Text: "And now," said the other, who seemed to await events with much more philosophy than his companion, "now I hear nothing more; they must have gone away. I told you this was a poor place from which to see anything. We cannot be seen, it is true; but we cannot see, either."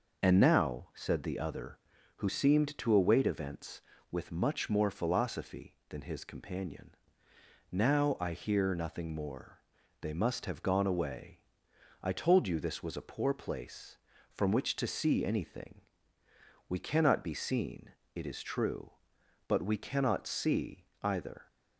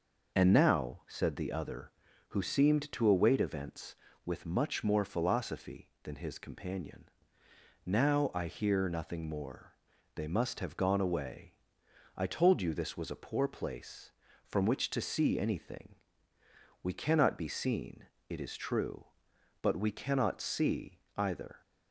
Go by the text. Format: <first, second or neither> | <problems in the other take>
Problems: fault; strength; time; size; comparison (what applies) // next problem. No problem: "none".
neither | none